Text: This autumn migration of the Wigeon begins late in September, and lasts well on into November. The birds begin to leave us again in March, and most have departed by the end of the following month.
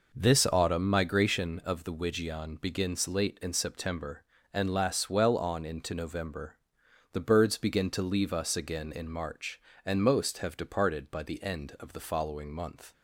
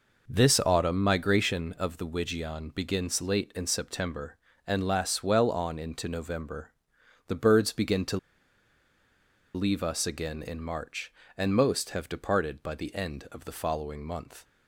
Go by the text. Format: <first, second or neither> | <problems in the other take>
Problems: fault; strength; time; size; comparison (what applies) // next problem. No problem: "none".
first | pauses between "to" and "leave"; strong; at 8.1 s; 1.3 s long